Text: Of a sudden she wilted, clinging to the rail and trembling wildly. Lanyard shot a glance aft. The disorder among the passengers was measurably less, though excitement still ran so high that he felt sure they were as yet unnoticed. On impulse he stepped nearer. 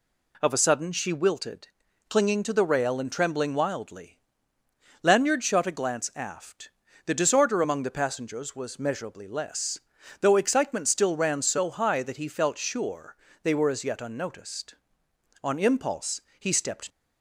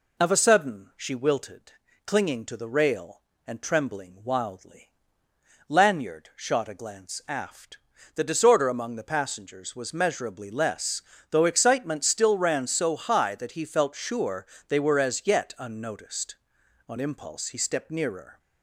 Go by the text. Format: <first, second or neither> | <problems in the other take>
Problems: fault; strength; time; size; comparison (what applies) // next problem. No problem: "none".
second | pauses between "sure" and "they"; slight; at 13.1 s; 0.26 s long; slight in the second // pauses between "impulse" and "he"; slight; at 16.1 s; 0.20 s long // stops before "nearer"; at 16.8 s